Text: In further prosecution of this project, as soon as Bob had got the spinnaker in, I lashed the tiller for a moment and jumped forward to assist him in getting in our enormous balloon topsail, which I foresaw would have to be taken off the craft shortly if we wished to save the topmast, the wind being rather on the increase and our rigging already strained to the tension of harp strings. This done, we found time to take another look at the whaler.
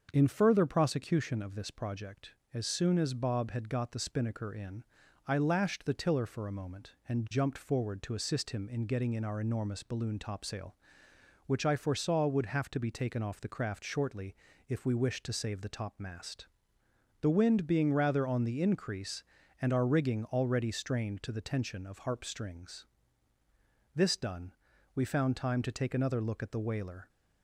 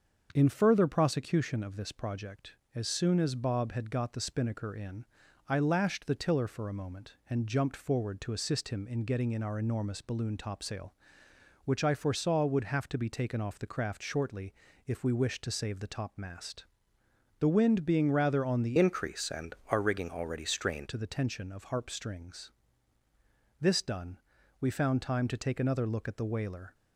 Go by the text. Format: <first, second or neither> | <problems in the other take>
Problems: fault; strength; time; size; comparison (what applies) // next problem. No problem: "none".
first | starts louder than the rest; until 1.3 s; 6.5 dB; also in the first // pauses between "shortly" and "if"; slight; at 14.5 s; 0.34 s long; slight in the first // changes voice from "increase" to "strained"; from 18.7 to 20.8 s; 2.1 s long